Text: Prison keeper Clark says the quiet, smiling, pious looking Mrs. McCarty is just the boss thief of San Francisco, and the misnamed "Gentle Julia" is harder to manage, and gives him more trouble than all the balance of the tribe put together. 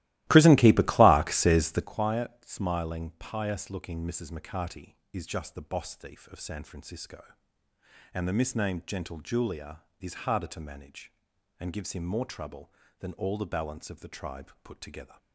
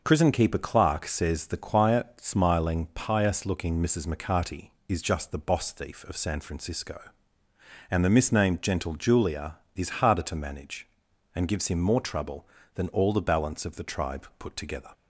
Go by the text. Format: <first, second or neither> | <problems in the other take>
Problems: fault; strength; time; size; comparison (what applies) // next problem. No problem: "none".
second | starts louder than the rest; strong; until 1.9 s; 16.5 dB